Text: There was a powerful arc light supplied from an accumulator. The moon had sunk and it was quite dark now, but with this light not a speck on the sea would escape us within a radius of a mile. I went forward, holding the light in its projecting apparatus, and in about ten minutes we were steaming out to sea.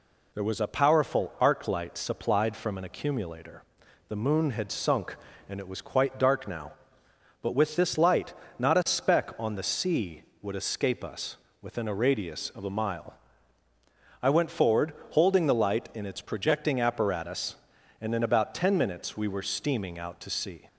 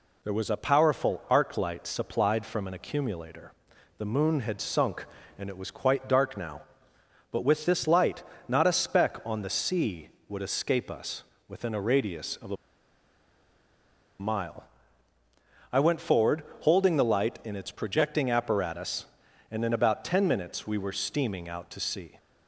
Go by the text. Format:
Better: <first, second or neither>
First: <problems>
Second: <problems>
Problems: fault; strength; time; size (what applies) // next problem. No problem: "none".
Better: first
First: pauses between "light" and "not"; slight; at 8.3 s; 0.26 s long // pauses between "us" and "within"; slight; at 11.3 s; 0.24 s long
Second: pauses between "light" and "not"; slight; at 8.2 s; 0.26 s long // pauses between "us" and "within"; slight; at 11.2 s; 0.24 s long // pauses between "a" and "mile"; strong; at 12.5 s; 1.6 s long